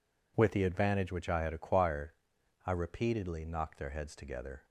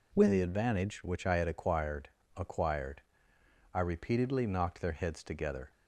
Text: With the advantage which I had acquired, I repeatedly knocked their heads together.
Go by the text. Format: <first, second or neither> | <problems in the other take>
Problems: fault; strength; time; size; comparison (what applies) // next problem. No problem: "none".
first | says "acquired" twice; at 2.3 s